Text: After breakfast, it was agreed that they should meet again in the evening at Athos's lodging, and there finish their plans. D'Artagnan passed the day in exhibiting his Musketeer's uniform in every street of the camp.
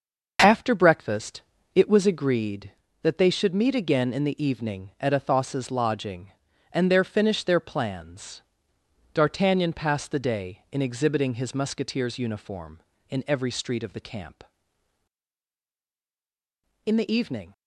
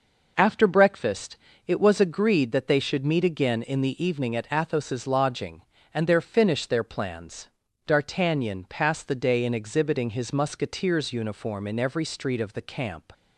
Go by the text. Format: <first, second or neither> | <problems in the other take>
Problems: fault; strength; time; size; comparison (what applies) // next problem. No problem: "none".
second | starts louder than the rest; noticeable; until 1.4 s; 6 dB // goes on to say "In the evening"; noticeable; from 16.8 s on; 0.66 s long